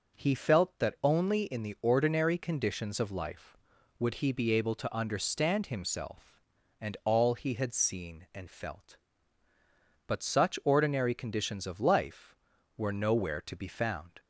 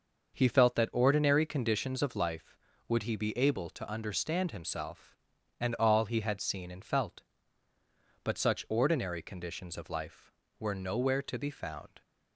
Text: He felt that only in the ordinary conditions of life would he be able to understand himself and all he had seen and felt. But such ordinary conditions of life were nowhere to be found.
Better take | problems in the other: first | starts louder than the rest; noticeable; until 1.3 s; 6 dB; noticeable in the first // skips "only in the"; at 0.8 s

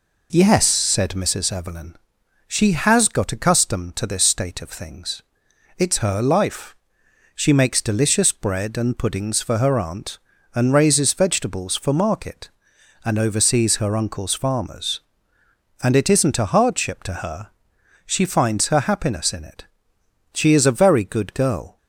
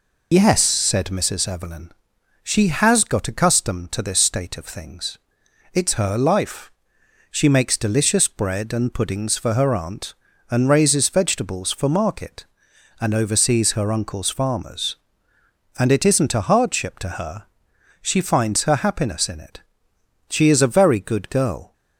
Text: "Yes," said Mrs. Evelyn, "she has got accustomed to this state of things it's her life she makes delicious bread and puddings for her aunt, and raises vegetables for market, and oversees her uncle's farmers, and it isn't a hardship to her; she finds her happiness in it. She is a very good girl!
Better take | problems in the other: first | loses the start of "Yes"; at 0.3 s; 55 ms // pauses between "things" and "it's"; noticeable; at 5.1 s; 0.56 s long; noticeable in the first // pauses between "life" and "she"; noticeable; at 6.7 s; 0.60 s long; noticeable in the first

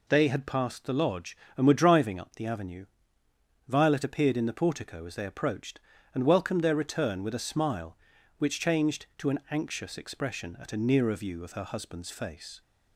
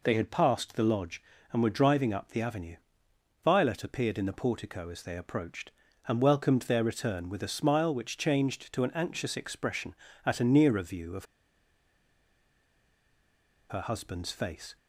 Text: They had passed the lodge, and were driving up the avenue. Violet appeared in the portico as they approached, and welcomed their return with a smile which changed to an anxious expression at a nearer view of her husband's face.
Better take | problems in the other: first | pauses between "of" and "her"; strong; at 11.2 s; 2.4 s long

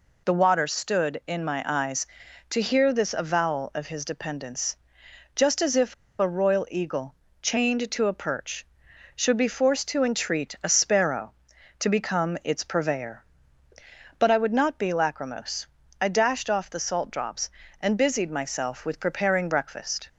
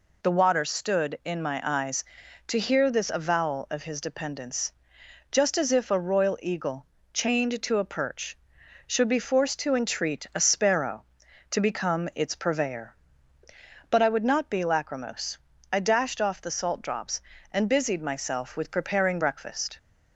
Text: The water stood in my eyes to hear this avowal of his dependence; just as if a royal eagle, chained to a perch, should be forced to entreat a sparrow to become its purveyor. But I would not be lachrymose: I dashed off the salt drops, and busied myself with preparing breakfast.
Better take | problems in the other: second | pauses between "if" and "a"; slight; at 5.9 s; 0.25 s long

